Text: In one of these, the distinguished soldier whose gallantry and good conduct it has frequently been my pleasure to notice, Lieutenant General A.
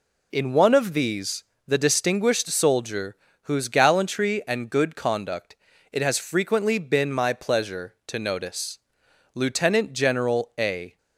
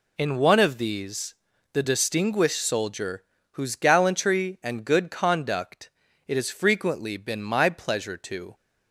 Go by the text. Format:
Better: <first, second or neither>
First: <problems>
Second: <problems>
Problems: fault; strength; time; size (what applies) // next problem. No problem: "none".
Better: first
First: pauses between "soldier" and "whose"; slight; at 3.1 s; 0.26 s long // pauses between "conduct" and "it"; slight; at 5.5 s; 0.34 s long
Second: pauses between "soldier" and "whose"; slight; at 3.2 s; 0.28 s long // pauses between "conduct" and "it"; slight; at 5.8 s; 0.36 s long // stops before "notice Lieutenant General A"; at 8.5 s